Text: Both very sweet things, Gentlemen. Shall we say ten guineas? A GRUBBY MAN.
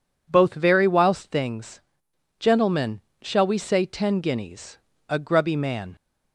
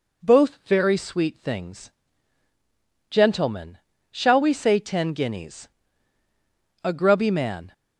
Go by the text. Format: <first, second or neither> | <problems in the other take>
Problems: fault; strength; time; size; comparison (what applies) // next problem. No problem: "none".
second | says "whilst" for "sweet"; at 0.8 s